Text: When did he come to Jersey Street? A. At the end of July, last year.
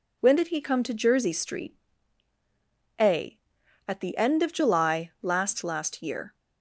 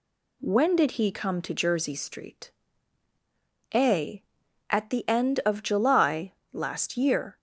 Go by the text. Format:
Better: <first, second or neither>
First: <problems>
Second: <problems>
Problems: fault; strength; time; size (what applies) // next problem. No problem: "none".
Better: second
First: says "last" twice; at 5.6 s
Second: none